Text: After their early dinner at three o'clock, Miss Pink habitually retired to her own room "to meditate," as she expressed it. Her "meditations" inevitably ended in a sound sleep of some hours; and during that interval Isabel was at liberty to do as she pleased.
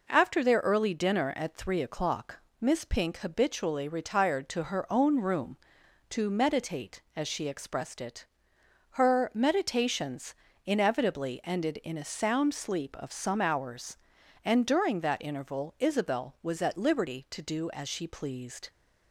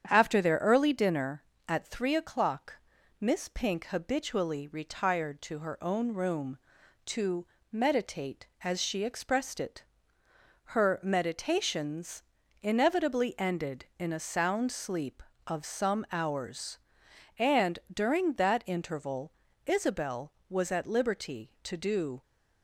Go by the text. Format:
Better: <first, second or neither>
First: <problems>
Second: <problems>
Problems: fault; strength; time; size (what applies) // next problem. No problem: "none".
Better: first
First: pauses between "meditations" and "inevitably"; slight; at 10.3 s; 0.30 s long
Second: starts louder than the rest; strong; until 1.1 s; 8.5 dB // pauses between "to" and "meditate"; slight; at 7.4 s; 0.24 s long // pauses between "meditations" and "inevitably"; at 12.2 s; 0.40 s long // pauses between "interval" and "Isabel"; slight; at 19.3 s; 0.34 s long // stops before "as she pleased"; at 22.2 s